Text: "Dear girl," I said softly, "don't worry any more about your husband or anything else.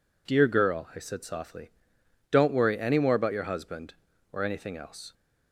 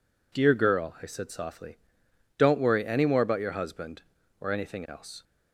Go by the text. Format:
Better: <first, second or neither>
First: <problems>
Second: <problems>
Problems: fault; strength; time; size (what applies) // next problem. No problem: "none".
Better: neither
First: none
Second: none